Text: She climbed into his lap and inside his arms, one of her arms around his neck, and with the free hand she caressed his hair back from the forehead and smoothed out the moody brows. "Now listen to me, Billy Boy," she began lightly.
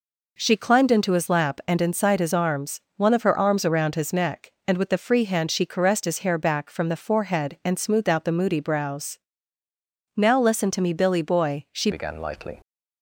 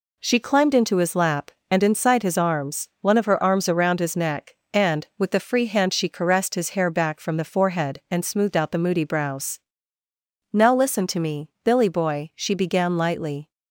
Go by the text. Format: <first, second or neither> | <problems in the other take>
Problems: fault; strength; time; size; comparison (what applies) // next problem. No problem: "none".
second | changes voice at "began"; from 11.9 s on; 0.7 s long